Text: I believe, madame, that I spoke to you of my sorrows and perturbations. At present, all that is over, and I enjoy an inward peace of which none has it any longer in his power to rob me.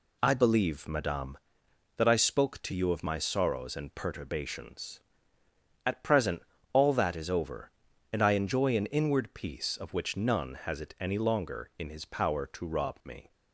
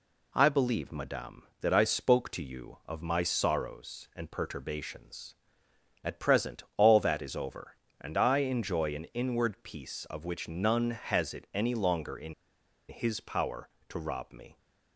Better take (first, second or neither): first